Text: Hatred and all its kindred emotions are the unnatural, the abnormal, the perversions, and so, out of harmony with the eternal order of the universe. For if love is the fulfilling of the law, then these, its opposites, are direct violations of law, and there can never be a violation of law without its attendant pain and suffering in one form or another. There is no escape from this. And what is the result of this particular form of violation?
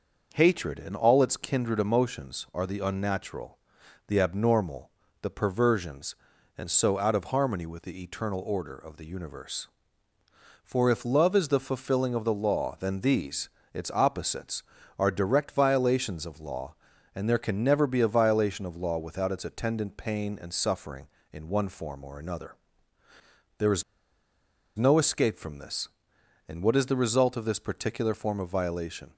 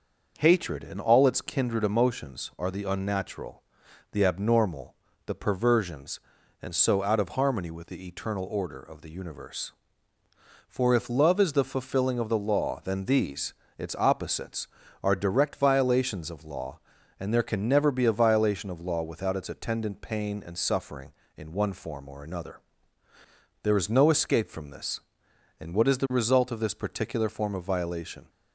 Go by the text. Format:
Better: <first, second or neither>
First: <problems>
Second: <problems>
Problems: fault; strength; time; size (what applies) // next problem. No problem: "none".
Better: second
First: starts louder than the rest; noticeable; until 1.3 s; 6 dB // pauses between "is" and "no"; noticeable; at 23.8 s; 0.95 s long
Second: starts louder than the rest; noticeable; until 1.3 s; 6 dB